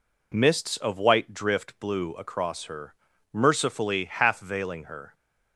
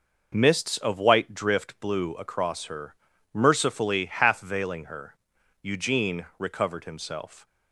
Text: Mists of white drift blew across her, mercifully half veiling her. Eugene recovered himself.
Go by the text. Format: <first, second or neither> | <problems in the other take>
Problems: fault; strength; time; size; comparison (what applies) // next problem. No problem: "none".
second | stops before "Eugene recovered himself"; at 5.1 s